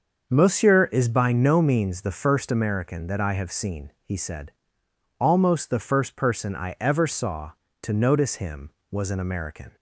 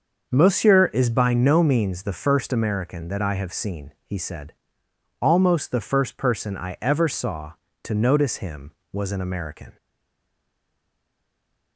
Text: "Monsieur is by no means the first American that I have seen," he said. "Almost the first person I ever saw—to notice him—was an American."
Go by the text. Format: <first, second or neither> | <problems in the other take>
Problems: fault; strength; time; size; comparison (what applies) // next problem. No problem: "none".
first | starts louder than the rest; until 1.3 s; 6.5 dB; also in the first // stays silent after the last word; noticeable; from 9.7 s on; 2.0 s long